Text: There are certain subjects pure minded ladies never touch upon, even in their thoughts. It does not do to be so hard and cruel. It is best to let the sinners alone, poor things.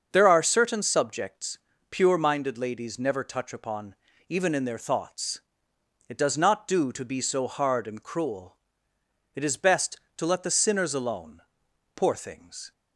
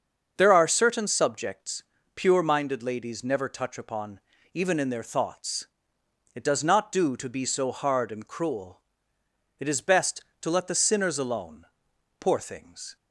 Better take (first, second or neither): neither